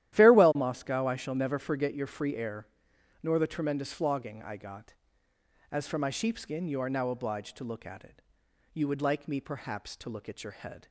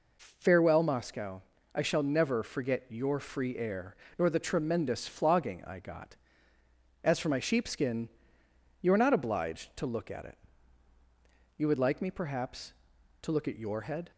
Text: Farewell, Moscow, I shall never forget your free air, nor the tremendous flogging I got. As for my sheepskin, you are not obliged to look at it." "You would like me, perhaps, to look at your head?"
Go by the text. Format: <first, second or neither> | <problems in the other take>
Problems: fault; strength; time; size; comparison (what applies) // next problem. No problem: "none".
second | starts louder than the rest; strong; until 1.1 s; 13 dB // says "now" for "not"; at 6.8 s